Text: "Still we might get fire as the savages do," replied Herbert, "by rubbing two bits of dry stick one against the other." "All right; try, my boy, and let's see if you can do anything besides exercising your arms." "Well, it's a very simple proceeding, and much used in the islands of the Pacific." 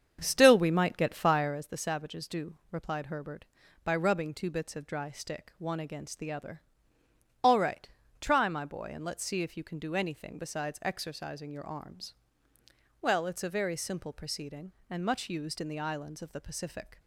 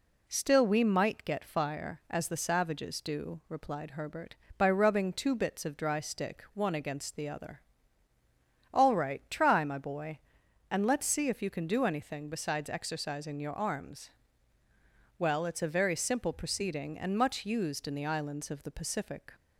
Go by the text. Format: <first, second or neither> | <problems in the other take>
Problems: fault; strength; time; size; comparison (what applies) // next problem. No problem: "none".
second | starts louder than the rest; strong; until 1.6 s; 7.5 dB